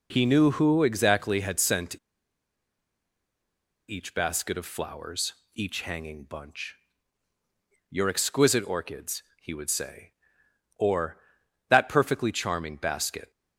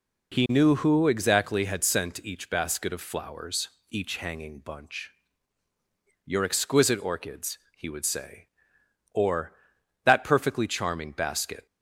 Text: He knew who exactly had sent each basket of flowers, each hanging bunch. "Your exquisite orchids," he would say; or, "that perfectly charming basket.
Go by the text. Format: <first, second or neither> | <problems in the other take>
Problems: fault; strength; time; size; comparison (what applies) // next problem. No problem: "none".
second | pauses between "sent" and "each"; strong; at 1.9 s; 1.9 s long